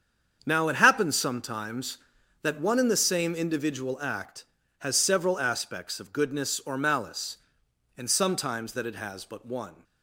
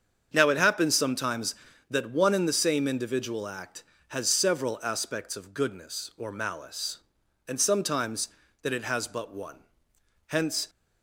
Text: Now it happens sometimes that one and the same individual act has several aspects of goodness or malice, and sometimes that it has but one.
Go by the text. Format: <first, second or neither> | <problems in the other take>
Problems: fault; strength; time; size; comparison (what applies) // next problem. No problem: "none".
first | starts louder than the rest; strong; until 1.3 s; 7 dB; strong in the first // goes on to say "Hence"; slight; from 10.2 s on; 0.42 s long